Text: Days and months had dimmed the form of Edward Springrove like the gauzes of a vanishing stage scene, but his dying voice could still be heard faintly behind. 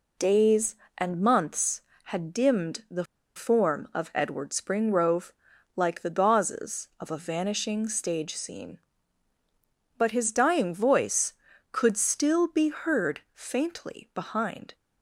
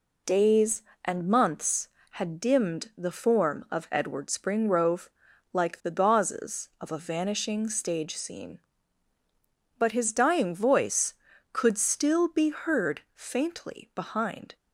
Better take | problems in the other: second | pauses between "the" and "form"; slight; at 3.0 s; 0.32 s long // pauses between "Springrove" and "like"; at 5.3 s; 0.44 s long; also in the second

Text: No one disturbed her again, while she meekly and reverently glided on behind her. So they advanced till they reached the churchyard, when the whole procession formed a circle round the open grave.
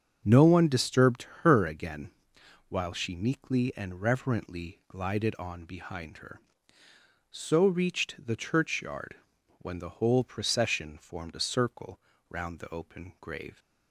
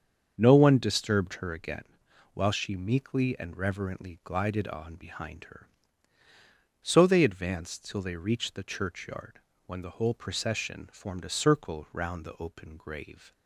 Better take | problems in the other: second | starts louder than the rest; strong; until 1.2 s; 7 dB; strong in the second // pauses between "disturbed" and "her"; slight; at 1.2 s; 0.16 s long // skips "they advanced till they"; at 7.6 s // pauses between "circle" and "round"; slight; at 11.9 s; 0.32 s long

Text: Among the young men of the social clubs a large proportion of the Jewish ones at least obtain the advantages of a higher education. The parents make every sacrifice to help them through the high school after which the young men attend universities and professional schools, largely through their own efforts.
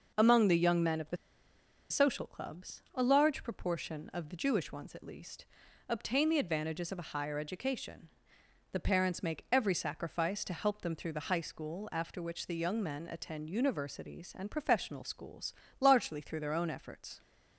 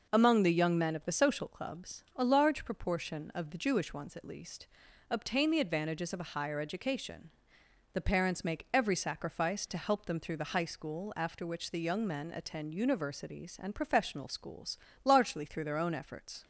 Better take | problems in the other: second | pauses between "the" and "social"; noticeable; at 1.1 s; 0.73 s long // pauses between "least" and "obtain"; at 5.4 s; 0.44 s long; also in the second

